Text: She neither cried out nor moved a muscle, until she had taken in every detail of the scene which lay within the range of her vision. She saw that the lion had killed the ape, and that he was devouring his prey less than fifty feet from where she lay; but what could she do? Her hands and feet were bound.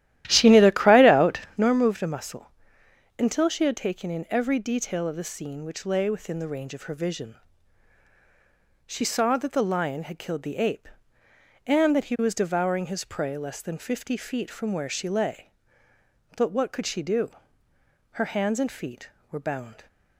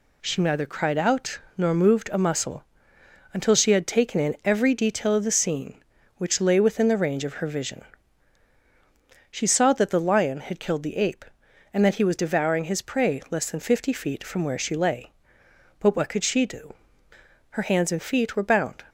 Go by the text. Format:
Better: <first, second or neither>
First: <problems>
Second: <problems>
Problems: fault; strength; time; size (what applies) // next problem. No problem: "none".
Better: second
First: starts louder than the rest; strong; until 1.7 s; 13.5 dB // pauses between "out" and "nor"; slight; at 1.3 s; 0.16 s long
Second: pauses between "out" and "nor"; slight; at 1.3 s; 0.18 s long